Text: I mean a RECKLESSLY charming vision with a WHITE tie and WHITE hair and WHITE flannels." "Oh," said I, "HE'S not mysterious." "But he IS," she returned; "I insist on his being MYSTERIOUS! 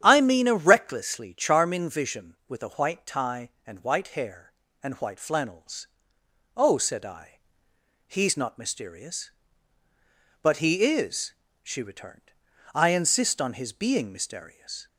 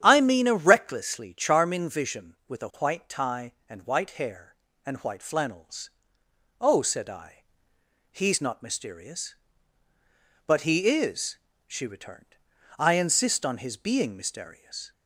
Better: neither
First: starts louder than the rest; strong; until 1.0 s; 9.5 dB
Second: starts louder than the rest; strong; until 1.0 s; 9.5 dB

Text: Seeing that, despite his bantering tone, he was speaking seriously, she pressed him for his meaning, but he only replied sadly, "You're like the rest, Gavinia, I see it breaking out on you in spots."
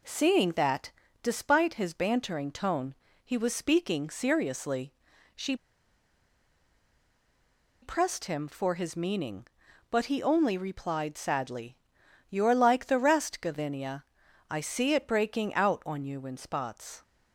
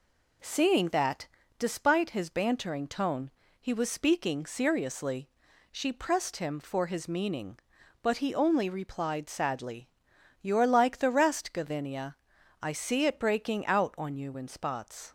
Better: second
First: pauses between "she" and "pressed"; strong; at 5.5 s; 2.2 s long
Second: none

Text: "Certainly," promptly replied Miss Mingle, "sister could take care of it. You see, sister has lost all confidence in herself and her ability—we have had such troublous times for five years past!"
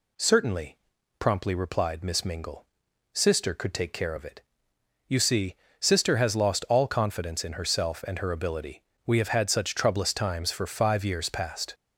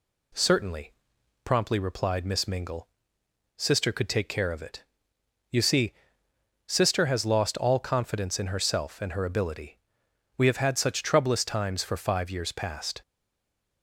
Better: first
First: none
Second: stays silent after the last word; slight; from 13.0 s on; 0.8 s long

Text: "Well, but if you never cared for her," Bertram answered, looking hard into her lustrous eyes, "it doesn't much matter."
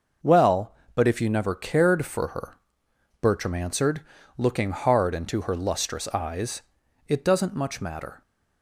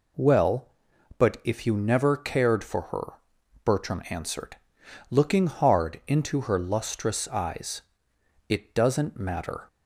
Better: first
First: none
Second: skips "much"; at 9.1 s

